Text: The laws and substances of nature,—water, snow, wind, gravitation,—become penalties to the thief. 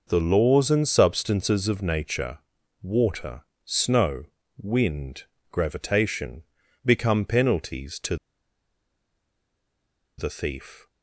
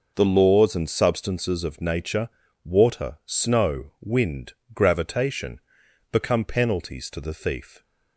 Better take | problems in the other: second | pauses between "to" and "the"; strong; at 8.1 s; 2.0 s long

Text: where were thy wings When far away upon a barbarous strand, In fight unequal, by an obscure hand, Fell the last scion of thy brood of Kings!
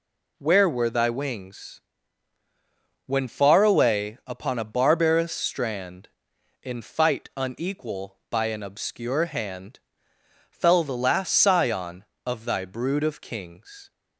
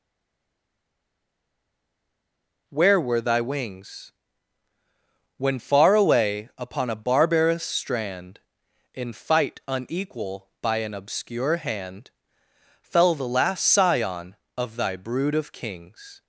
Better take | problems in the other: first | stays silent before the first word; strong; until 2.6 s; 2.6 s long // pauses between "wings" and "When"; strong; at 4.1 s; 1.2 s long; strong in the first

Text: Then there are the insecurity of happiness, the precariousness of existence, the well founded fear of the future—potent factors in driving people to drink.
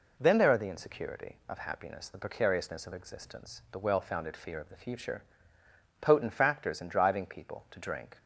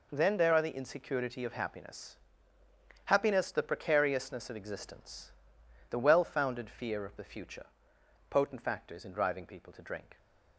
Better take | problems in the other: first | says "happiness" twice; at 3.0 s

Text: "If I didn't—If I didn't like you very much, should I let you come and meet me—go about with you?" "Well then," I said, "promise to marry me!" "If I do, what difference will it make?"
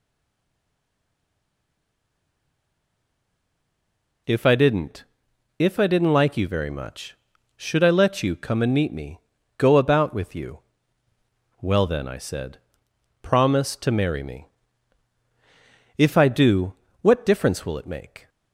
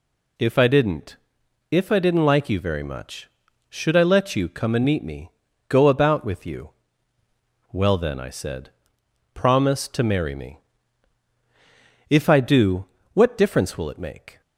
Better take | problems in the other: second | stays silent before the first word; strong; until 4.2 s; 4.2 s long

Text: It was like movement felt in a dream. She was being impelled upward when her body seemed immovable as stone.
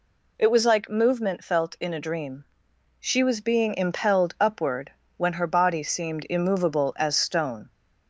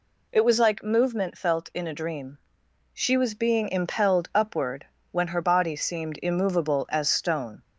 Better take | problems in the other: neither | pauses between "upward" and "when"; slight; the same in both

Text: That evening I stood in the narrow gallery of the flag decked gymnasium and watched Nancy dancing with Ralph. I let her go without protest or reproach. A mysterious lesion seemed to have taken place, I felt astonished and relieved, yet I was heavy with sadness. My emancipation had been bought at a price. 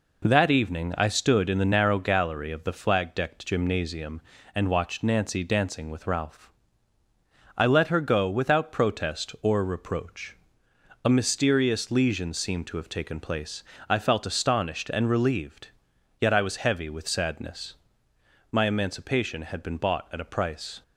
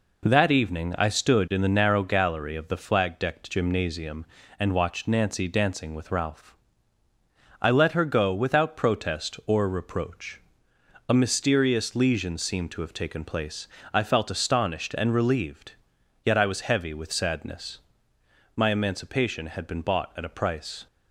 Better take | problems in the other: neither | none

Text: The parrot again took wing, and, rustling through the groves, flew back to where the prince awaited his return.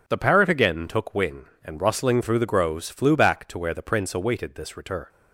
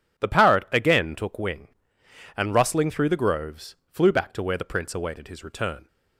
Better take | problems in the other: second | says "this" for "his"; at 4.5 s

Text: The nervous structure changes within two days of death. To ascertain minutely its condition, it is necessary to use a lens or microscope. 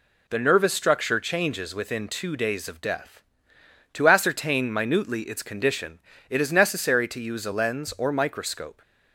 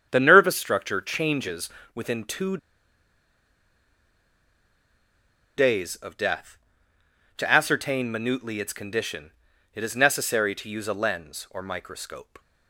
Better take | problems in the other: first | starts louder than the rest; strong; until 1.1 s; 8 dB // pauses between "changes" and "within"; slight; at 1.6 s; 0.24 s long // pauses between "two" and "days"; strong; at 2.5 s; 3.0 s long

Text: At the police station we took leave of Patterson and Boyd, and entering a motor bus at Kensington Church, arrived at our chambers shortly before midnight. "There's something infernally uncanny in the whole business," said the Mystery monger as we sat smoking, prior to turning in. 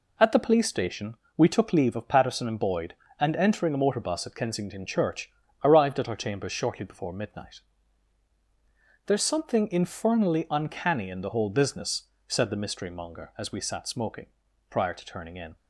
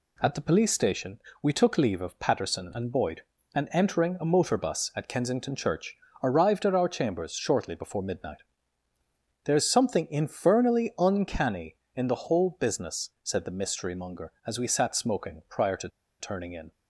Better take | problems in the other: first | pauses between "station" and "we"; slight; at 1.1 s; 0.24 s long; slight in the first // pauses between "to" and "turning"; slight; at 15.8 s; 0.32 s long

